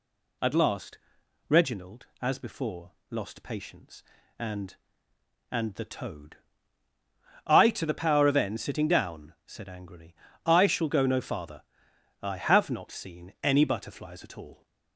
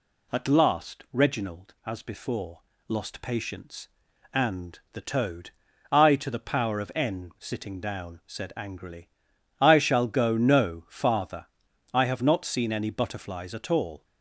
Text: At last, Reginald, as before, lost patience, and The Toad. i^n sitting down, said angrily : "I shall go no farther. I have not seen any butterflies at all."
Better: second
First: says "and" twice; at 5.5 s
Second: none

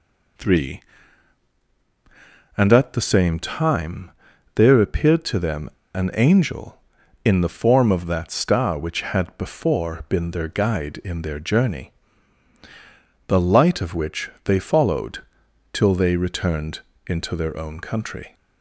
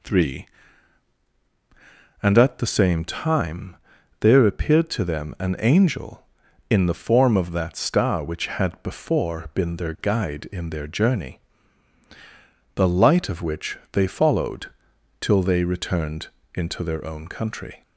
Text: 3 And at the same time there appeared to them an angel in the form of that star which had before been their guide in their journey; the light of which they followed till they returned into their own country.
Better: second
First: pauses between "time" and "there"; noticeable; at 4.0 s; 0.46 s long // pauses between "them" and "an"; slight; at 5.6 s; 0.24 s long // pauses between "followed" and "till"; noticeable; at 15.1 s; 0.52 s long // pauses between "returned" and "into"; slight; at 16.7 s; 0.26 s long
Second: pauses between "time" and "there"; noticeable; at 3.7 s; 0.46 s long // pauses between "followed" and "till"; noticeable; at 14.6 s; 0.52 s long // pauses between "returned" and "into"; slight; at 16.2 s; 0.26 s long

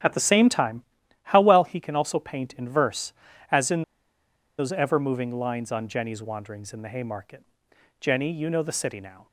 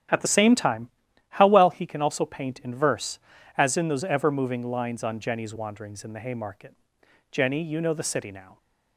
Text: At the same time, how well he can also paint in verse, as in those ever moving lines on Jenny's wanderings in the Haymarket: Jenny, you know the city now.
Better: second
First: starts louder than the rest; strong; until 1.4 s; 9.5 dB // pauses between "in" and "those"; noticeable; at 3.8 s; 0.76 s long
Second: starts louder than the rest; strong; until 1.5 s; 9 dB

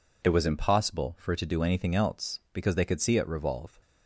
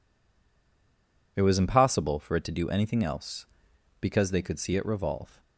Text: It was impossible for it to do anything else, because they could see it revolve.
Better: first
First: none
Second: stays silent before the first word; noticeable; until 1.3 s; 1.3 s long

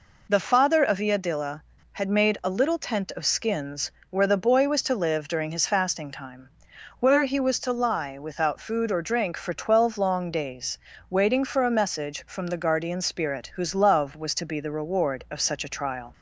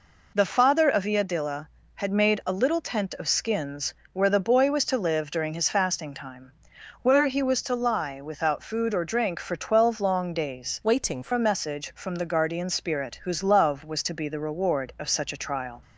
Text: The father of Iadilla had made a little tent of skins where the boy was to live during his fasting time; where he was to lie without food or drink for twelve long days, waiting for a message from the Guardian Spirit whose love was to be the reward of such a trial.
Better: first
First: pauses between "skins" and "where"; slight; at 3.9 s; 0.18 s long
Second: pauses between "skins" and "where"; slight; at 3.9 s; 0.18 s long // changes voice from "waiting" to "for"; from 10.8 to 11.3 s; 0.5 s long

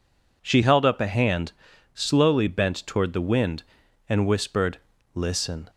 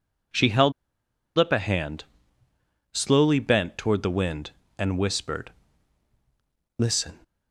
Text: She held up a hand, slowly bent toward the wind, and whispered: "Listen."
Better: first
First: none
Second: pauses between "held" and "up"; noticeable; at 0.7 s; 0.65 s long

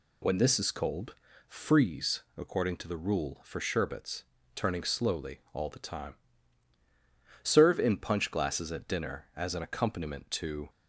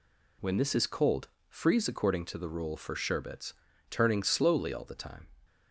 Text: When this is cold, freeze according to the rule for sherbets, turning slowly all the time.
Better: second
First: pauses between "freeze" and "according"; slight; at 2.2 s; 0.16 s long // goes on to say "Serve in punch glasses at dinner as an accompaniment to"; strong; from 7.4 s on; 3.2 s long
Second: none

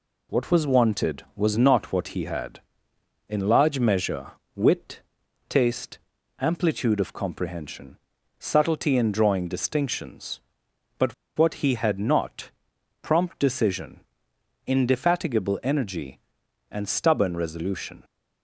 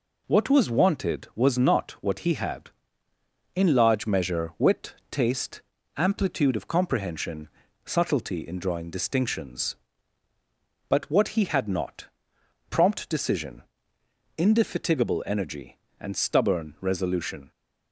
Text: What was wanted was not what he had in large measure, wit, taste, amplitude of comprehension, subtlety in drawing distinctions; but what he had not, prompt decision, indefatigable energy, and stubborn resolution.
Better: second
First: pauses between "but" and "what"; slight; at 11.1 s; 0.24 s long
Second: none

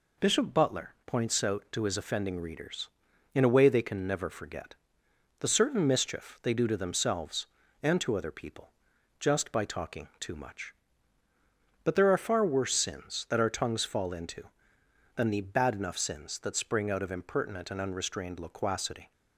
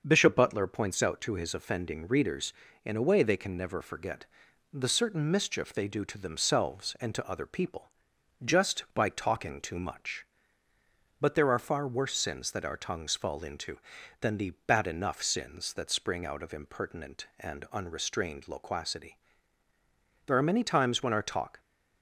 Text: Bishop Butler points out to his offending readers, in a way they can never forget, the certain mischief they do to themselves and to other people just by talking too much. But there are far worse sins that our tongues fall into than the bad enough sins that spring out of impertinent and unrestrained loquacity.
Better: first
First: pauses between "people" and "just"; noticeable; at 8.7 s; 0.48 s long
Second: starts louder than the rest; until 1.0 s; 6.5 dB // pauses between "people" and "just"; noticeable; at 7.9 s; 0.54 s long // pauses between "the" and "bad"; slight; at 14.5 s; 0.16 s long // goes on to say "There are many times when our talk"; from 20.2 s on; 1.3 s long

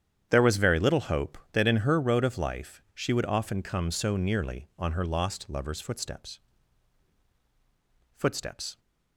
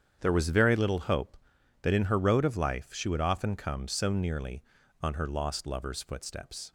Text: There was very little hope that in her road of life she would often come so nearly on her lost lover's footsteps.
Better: second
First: starts louder than the rest; strong; until 1.3 s; 9 dB // says "footsteps" twice; at 8.1 s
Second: starts louder than the rest; strong; until 1.2 s; 8.5 dB

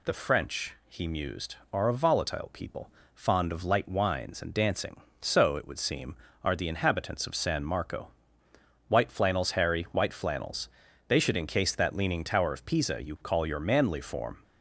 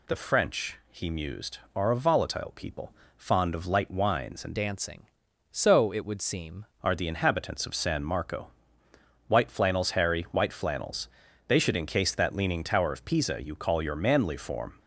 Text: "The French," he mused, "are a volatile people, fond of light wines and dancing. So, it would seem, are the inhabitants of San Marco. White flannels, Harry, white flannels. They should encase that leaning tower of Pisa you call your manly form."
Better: first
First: none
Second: changes voice from "dancing" to "seem"; from 4.5 to 6.6 s; 2.1 s long

